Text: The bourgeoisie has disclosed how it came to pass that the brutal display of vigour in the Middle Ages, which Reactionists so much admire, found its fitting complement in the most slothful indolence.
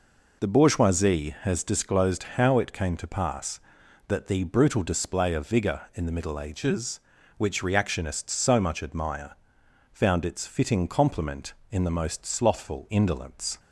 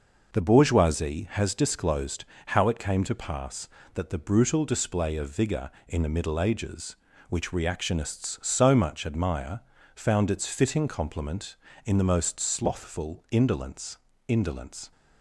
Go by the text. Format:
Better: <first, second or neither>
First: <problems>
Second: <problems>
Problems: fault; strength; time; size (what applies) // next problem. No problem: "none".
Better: first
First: none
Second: pauses between "disclosed" and "how"; slight; at 2.2 s; 0.24 s long // says "indolence" twice; at 14.2 s